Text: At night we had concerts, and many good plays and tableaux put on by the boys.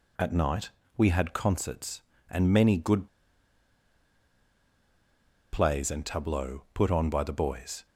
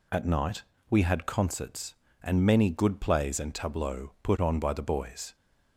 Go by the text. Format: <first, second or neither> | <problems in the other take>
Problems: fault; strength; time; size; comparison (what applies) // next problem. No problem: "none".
second | pauses between "night" and "we"; slight; at 0.6 s; 0.26 s long; slight in the second // pauses between "good" and "plays"; strong; at 3.0 s; 2.4 s long